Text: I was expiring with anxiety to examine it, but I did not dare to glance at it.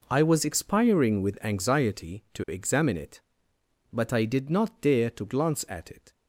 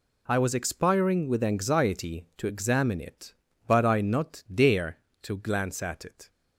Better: first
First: none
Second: skips "did"; at 4.0 s

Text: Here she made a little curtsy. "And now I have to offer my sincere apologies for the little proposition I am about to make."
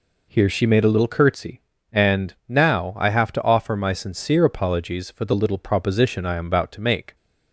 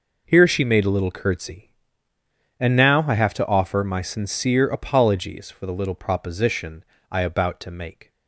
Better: first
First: none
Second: pauses between "proposition" and "I"; slight; at 6.8 s; 0.28 s long // skips "am"; at 7.2 s

